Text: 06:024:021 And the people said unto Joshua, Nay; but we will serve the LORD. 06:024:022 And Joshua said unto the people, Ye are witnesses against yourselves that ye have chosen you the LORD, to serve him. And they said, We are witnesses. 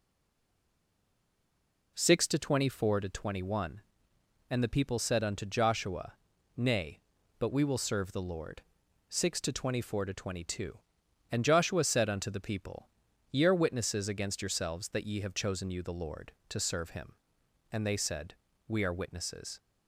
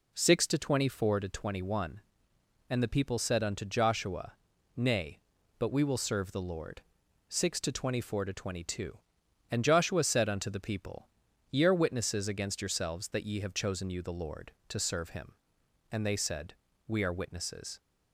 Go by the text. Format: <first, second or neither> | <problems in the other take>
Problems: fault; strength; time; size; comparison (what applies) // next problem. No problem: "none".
second | stays silent before the first word; noticeable; until 1.9 s; 1.9 s long